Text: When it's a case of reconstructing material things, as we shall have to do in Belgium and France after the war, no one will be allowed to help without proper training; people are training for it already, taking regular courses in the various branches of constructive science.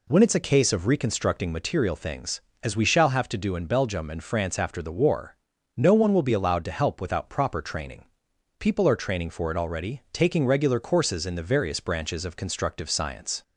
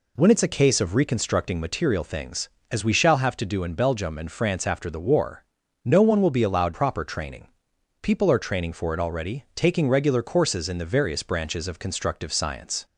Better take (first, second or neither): first